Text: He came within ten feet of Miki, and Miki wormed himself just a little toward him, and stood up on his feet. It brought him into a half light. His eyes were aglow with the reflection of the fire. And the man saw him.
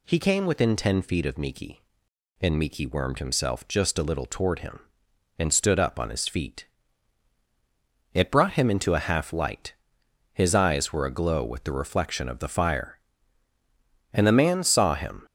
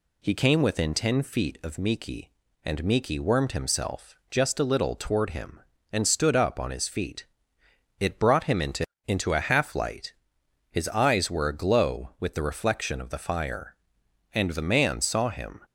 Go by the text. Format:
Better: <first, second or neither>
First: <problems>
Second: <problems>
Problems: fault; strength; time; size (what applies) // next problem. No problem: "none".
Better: first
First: none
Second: pauses between "himself" and "just"; slight; at 4.1 s; 0.16 s long // says "into" twice; at 9.0 s